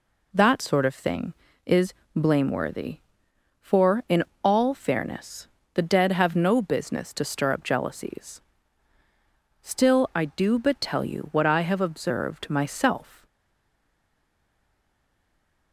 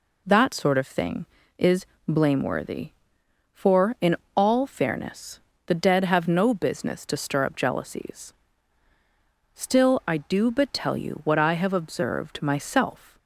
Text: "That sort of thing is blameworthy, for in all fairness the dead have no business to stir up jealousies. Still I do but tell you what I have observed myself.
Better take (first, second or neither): second